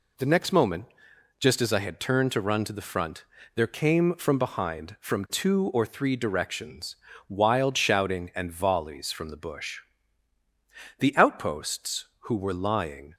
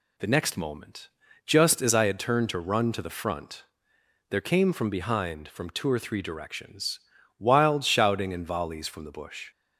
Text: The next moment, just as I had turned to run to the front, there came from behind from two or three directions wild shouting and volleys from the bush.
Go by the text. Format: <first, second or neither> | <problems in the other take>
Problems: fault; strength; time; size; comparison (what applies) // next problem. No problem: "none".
second | pauses between "directions" and "wild"; slight; at 6.9 s; 0.32 s long; also in the second // goes on to say "The outposts who were lying"; strong; from 10.9 s on; 2.1 s long